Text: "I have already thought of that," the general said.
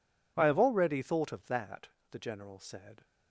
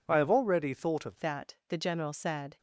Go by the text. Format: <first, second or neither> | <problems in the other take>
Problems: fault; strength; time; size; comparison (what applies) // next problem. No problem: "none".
first | changes voice at "that"; from 1.2 s on; 1.3 s long